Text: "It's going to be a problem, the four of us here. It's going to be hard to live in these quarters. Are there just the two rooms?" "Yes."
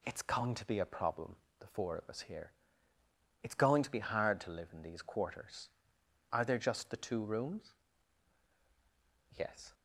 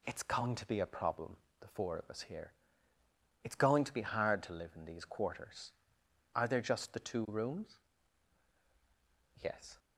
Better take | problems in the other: neither | none

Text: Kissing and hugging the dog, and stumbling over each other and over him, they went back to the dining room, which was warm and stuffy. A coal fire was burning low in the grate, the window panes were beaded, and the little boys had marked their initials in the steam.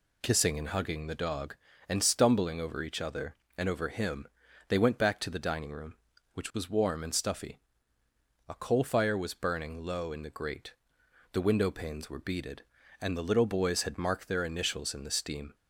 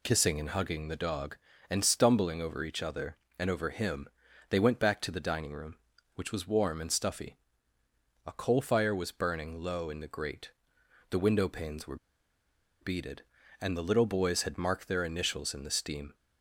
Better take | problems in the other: first | pauses between "were" and "beaded"; noticeable; at 11.9 s; 0.85 s long

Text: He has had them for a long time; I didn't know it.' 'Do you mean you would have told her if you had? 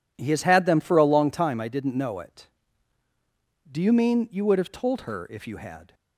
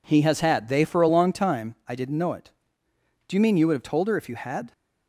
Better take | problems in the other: first | says "they" for "them"; at 0.6 s

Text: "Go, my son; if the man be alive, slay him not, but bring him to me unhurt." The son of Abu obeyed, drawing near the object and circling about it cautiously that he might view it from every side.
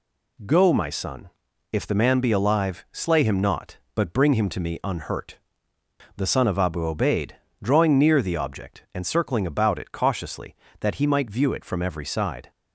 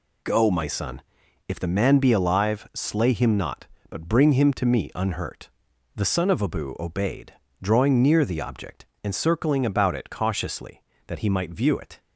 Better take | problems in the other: first | stops before "from every side"; at 12.0 s

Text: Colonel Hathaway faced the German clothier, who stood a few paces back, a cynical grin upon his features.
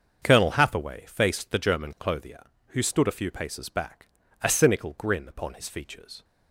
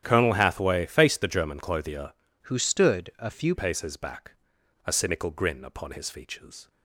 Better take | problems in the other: first | starts louder than the rest; strong; until 1.0 s; 10 dB; also in the first // changes voice from "who" to "few"; from 2.4 to 3.5 s; 1.1 s long

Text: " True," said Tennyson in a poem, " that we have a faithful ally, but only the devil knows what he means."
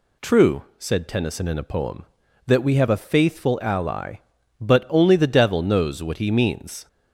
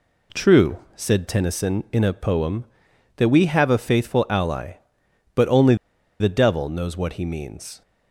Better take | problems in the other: first | pauses between "only" and "the"; at 5.7 s; 0.45 s long

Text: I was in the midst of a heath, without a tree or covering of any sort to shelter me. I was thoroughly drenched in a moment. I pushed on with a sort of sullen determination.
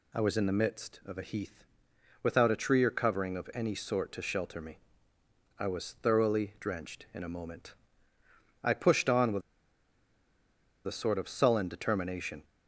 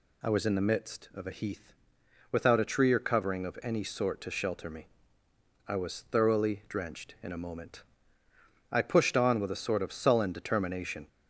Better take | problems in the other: second | pauses between "with" and "a"; strong; at 9.4 s; 1.4 s long

